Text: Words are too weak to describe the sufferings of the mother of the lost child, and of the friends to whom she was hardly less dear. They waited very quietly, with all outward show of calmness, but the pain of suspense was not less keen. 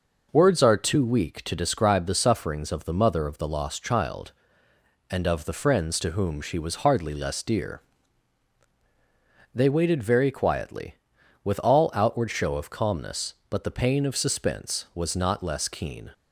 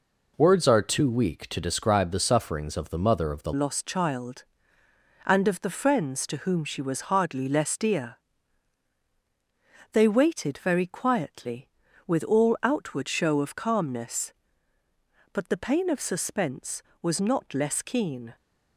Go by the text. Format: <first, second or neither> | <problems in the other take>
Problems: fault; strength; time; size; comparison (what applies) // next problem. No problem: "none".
first | changes voice at "lost"; from 3.5 s on; 14.8 s long